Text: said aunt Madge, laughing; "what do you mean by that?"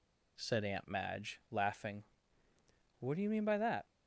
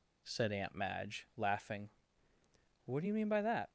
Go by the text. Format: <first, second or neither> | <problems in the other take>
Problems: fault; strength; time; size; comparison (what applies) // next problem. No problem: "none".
neither | none